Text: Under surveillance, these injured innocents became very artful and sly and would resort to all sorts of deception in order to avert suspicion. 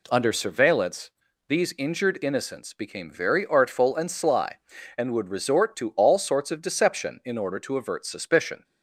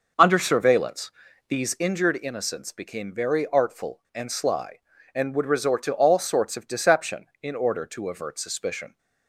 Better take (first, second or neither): first